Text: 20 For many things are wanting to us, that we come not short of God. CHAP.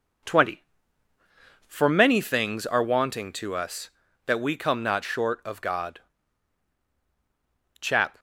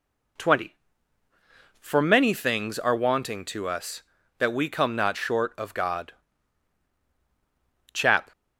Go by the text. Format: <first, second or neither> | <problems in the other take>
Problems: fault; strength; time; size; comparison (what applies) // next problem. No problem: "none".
second | gets quieter; slight; throughout; 3.5 dB